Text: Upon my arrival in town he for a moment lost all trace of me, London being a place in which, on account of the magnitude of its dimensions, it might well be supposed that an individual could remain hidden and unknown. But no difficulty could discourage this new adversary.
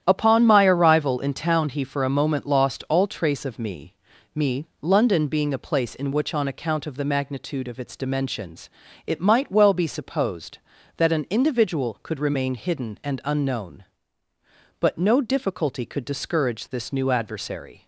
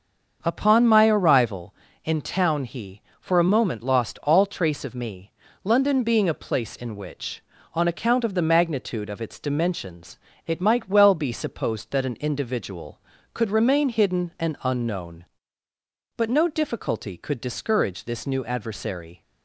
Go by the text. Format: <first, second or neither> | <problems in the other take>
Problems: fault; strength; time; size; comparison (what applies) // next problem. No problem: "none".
second | starts louder than the rest; strong; until 1.0 s; 10.5 dB; also in the second // says "me" twice; at 4.3 s